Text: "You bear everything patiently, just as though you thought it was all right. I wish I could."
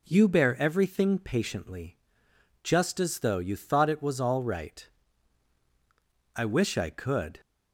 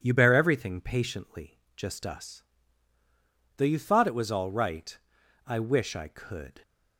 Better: first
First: none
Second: says "us" for "as"; at 2.0 s

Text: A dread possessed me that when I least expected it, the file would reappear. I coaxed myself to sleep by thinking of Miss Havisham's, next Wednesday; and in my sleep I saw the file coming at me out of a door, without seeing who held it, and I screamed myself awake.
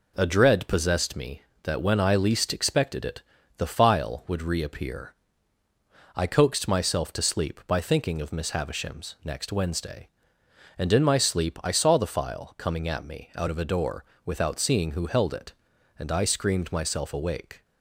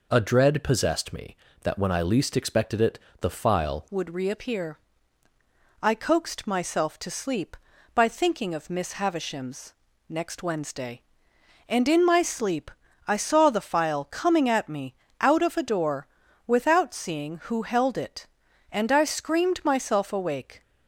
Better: first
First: none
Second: changes voice at "would"; from 3.8 s on; 16.8 s long // pauses between "sleep" and "I"; slight; at 12.7 s; 0.36 s long // pauses between "me" and "out"; slight; at 14.9 s; 0.26 s long

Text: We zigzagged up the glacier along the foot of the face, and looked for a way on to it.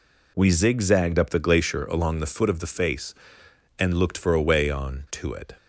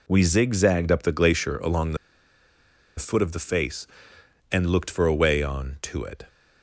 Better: first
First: none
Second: pauses between "the" and "foot"; at 1.9 s; 1.0 s long

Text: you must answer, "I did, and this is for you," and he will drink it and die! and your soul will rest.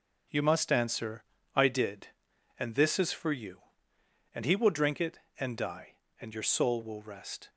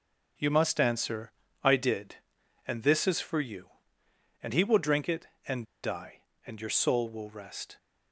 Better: first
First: none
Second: pauses between "and" and "die"; slight; at 5.6 s; 0.17 s long

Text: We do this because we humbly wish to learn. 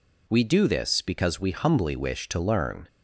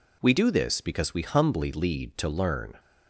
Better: first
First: none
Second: says "lead" for "wish"; at 1.7 s

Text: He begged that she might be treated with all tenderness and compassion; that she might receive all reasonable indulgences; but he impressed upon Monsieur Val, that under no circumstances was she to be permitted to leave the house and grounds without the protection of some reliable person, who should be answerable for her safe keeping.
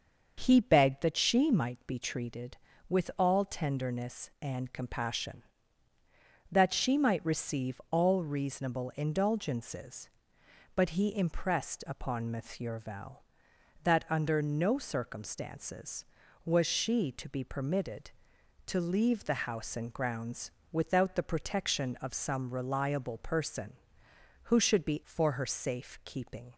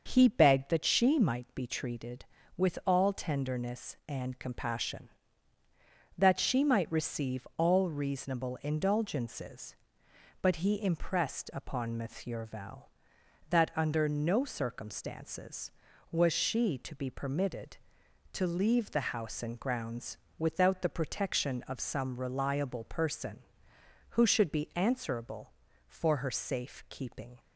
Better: second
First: starts louder than the rest; until 1.3 s; 6.5 dB // pauses between "grounds" and "without"; slight; at 20.5 s; 0.18 s long // skips "answerable"; at 25.0 s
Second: starts louder than the rest; until 1.0 s; 6.5 dB // pauses between "grounds" and "without"; slight; at 20.1 s; 0.18 s long

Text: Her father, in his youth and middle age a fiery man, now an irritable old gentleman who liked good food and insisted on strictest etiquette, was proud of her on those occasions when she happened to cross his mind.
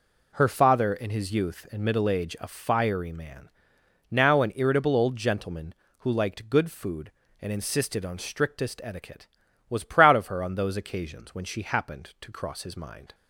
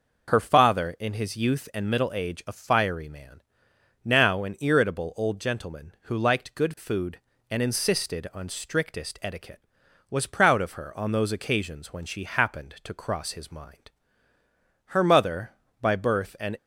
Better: first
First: none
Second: goes on to say "Her mother by birth an"; strong; from 14.8 s on; 1.7 s long

